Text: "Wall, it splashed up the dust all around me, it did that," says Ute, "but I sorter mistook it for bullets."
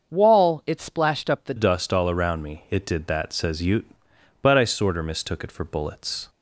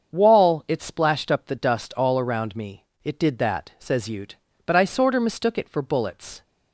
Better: second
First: starts louder than the rest; until 1.1 s; 6.5 dB // changes voice at "dust"; from 1.5 s on; 4.7 s long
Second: starts louder than the rest; until 1.1 s; 7 dB

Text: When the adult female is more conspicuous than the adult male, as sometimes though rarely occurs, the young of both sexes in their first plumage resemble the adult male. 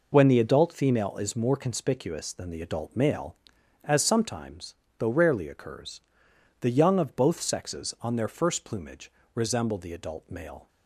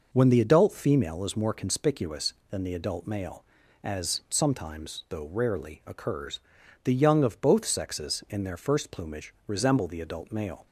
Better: second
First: pauses between "sometimes" and "though"; slight; at 4.7 s; 0.24 s long // says "on" for "in"; at 7.9 s // pauses between "plumage" and "resemble"; slight; at 9.0 s; 0.24 s long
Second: pauses between "plumage" and "resemble"; slight; at 9.3 s; 0.16 s long

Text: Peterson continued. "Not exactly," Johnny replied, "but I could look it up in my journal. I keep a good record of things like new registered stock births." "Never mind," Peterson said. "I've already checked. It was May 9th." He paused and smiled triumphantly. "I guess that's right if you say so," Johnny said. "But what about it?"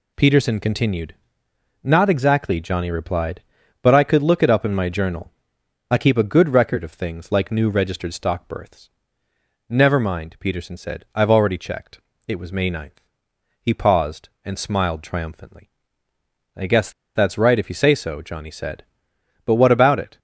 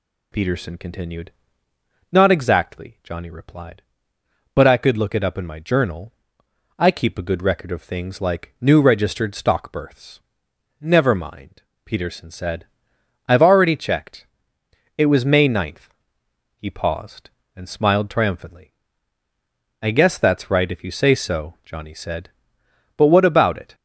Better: second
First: pauses between "guess" and "that's"; slight; at 16.9 s; 0.23 s long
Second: none

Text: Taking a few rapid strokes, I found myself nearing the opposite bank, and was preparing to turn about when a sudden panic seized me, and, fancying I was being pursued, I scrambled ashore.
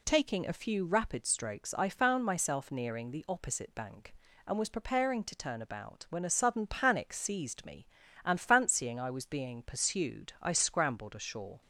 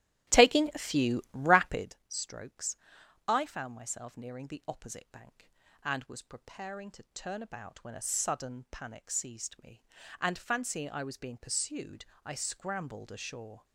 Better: first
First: none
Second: starts louder than the rest; strong; until 2.0 s; 13.5 dB

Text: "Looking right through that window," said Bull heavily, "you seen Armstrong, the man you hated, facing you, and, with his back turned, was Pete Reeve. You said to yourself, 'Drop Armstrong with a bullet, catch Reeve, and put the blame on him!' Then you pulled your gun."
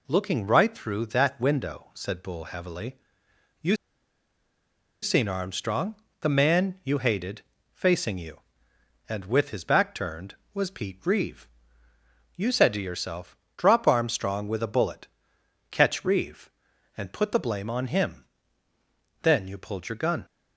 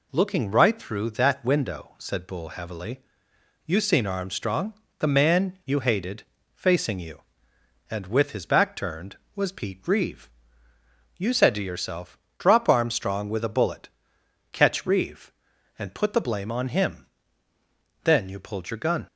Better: second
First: pauses between "you" and "seen"; strong; at 3.7 s; 1.2 s long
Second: none

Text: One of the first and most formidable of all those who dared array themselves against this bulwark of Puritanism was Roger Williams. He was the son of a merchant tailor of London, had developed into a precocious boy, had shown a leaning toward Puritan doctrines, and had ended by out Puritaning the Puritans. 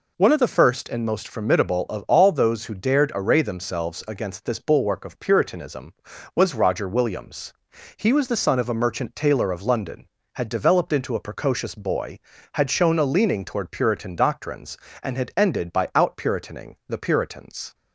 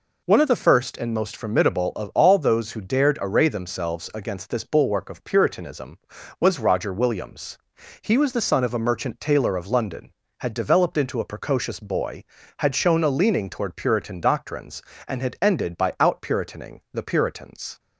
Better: neither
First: none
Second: none

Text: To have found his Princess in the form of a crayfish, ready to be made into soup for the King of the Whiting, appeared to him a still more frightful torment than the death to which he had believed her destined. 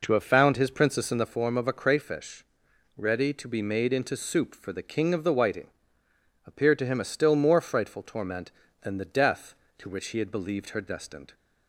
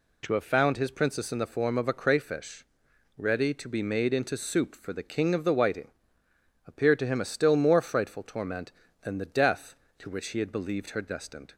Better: second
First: starts louder than the rest; noticeable; until 1.4 s; 4.5 dB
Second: none

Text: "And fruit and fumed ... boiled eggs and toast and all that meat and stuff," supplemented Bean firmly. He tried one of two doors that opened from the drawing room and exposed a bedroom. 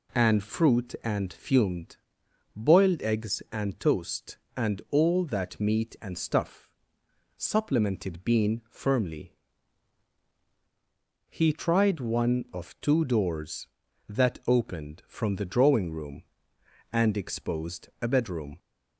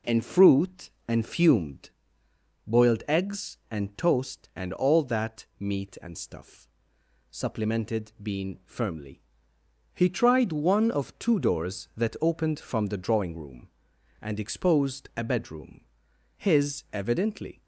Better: first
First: none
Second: goes on to say "His evidently"; noticeable; from 16.3 s on; 1.2 s long

